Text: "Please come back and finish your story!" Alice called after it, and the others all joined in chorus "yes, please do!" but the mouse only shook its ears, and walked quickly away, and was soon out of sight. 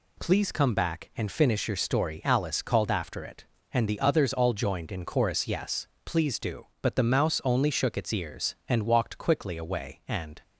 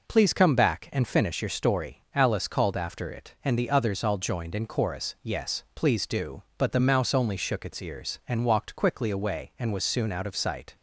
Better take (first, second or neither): second